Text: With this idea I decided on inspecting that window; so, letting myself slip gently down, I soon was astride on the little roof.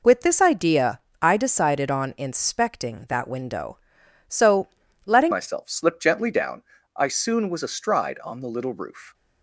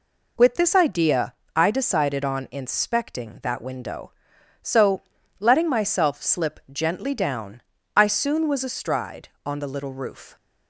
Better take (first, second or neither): second